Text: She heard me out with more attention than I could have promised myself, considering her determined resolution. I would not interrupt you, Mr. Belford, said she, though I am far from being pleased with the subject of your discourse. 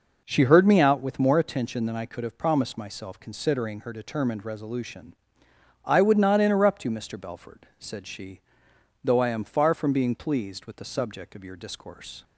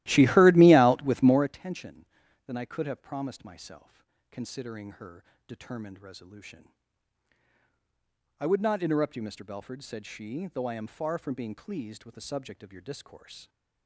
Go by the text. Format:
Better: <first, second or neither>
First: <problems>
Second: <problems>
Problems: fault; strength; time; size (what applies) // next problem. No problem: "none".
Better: first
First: none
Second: starts louder than the rest; strong; until 1.5 s; 16 dB // pauses between "her" and "determined"; slight; at 5.2 s; 0.24 s long